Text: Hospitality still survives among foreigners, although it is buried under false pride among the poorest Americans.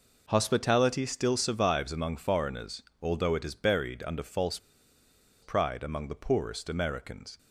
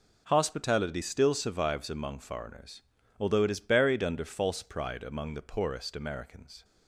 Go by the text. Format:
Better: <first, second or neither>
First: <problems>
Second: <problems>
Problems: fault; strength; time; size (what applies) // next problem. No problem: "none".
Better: second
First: pauses between "false" and "pride"; noticeable; at 4.5 s; 0.84 s long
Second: none